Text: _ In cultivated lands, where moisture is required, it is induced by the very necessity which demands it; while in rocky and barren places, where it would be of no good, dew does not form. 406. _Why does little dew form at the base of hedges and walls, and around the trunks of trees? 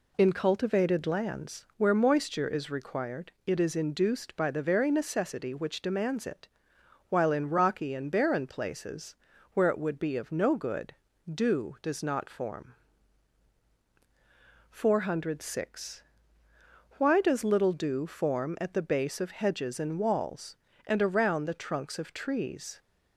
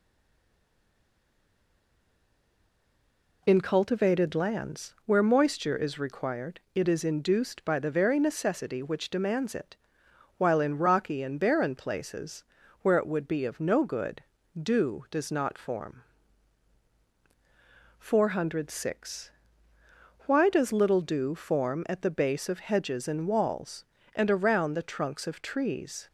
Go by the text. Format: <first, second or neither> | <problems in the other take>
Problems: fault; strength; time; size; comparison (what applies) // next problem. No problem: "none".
first | stays silent before the first word; strong; until 3.4 s; 3.4 s long